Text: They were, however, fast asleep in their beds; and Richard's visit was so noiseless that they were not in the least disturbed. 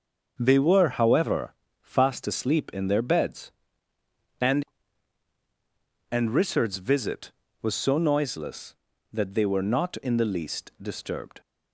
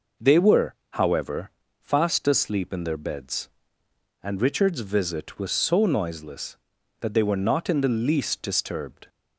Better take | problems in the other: second | starts louder than the rest; until 1.4 s; 6.5 dB // says "and" twice; at 6.1 s

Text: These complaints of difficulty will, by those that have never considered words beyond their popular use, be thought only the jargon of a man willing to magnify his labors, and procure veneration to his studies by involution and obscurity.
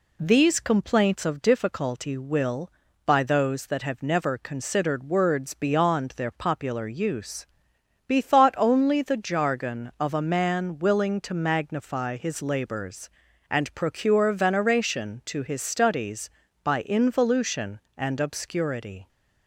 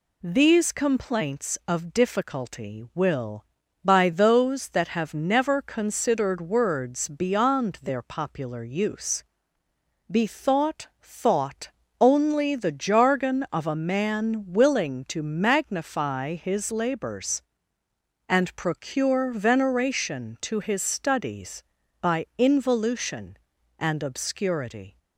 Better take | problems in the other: first | says "thought" twice; at 10.9 s

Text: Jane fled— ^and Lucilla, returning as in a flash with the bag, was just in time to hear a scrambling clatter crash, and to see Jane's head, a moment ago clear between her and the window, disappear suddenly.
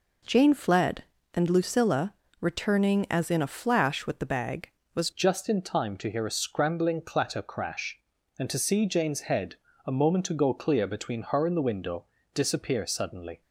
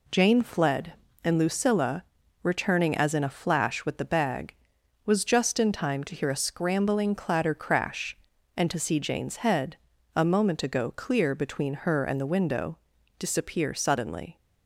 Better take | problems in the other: second | changes voice at "just"; from 5.1 s on; 8.3 s long

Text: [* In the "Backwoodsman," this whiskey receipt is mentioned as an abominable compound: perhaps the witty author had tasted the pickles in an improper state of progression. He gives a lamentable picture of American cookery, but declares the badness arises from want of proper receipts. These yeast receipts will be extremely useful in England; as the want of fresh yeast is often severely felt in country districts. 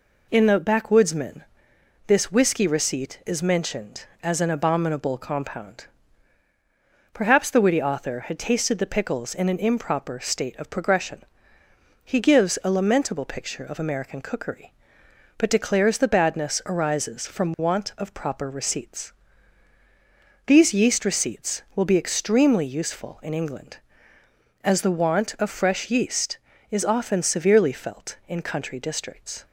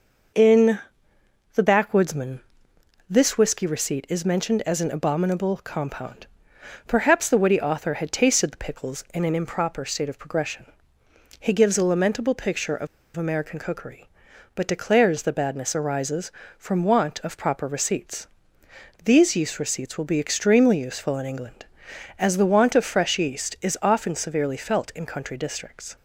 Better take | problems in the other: first | pauses between "In" and "the"; noticeable; at 0.7 s; 0.74 s long // pauses between "of" and "American"; slight; at 12.8 s; 0.28 s long

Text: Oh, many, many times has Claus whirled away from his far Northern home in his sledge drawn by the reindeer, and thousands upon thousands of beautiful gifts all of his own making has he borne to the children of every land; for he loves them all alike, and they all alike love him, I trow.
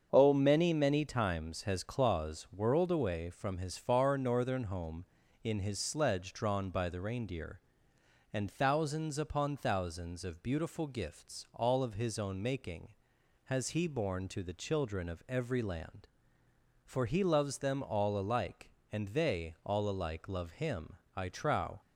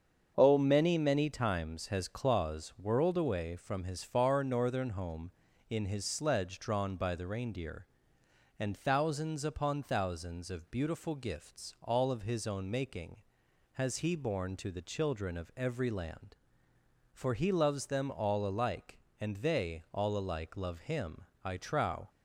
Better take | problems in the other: neither | starts louder than the rest; strong; the same in both

